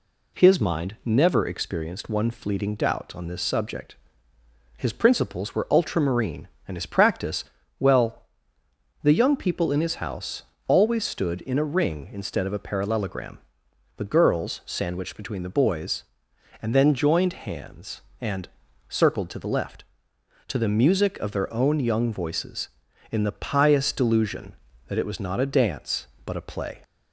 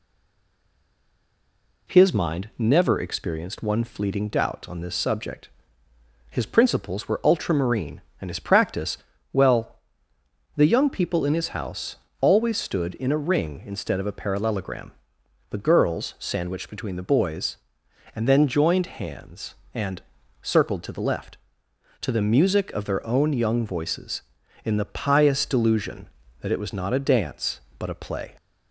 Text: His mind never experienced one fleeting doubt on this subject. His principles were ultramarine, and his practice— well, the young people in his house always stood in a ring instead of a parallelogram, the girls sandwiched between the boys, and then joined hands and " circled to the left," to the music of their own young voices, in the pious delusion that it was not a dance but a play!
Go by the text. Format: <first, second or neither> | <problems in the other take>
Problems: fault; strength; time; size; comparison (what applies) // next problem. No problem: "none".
first | stays silent before the first word; noticeable; until 1.8 s; 1.8 s long // pauses between "house" and "always"; slight; at 11.9 s; 0.24 s long; slight in the first